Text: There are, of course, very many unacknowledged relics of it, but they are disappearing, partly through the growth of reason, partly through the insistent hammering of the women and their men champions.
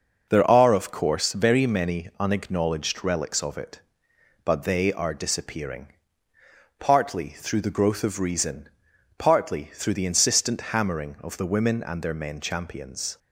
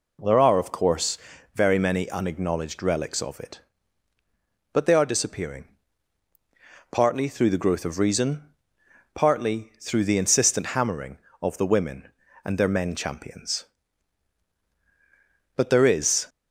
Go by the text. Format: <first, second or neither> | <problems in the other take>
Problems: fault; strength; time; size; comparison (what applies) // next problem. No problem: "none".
first | goes on to say "But there is"; noticeable; from 15.5 s on; 0.72 s long